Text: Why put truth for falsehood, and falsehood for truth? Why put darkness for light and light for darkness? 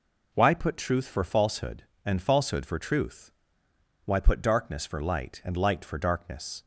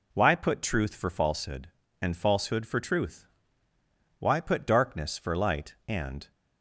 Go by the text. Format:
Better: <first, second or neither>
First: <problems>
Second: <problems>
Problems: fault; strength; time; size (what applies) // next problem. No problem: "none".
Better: first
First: none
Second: stops before "light for darkness"; at 6.3 s